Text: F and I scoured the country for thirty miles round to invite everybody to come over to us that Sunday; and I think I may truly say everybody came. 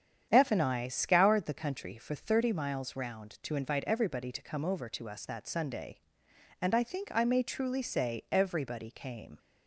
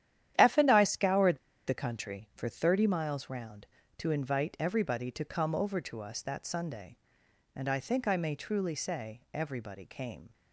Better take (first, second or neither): first